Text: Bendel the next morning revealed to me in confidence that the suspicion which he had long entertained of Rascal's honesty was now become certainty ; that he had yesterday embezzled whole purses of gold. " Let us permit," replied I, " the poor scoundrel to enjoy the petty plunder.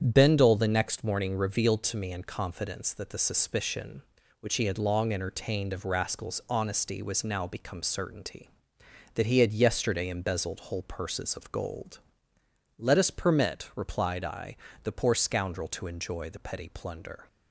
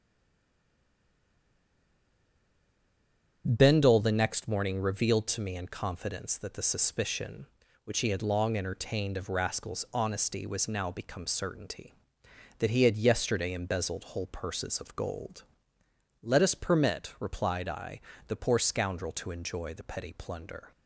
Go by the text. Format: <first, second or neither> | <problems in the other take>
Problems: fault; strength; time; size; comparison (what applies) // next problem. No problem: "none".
first | stays silent before the first word; strong; until 3.4 s; 3.4 s long // starts louder than the rest; strong; until 4.4 s; 8.5 dB; strong in the first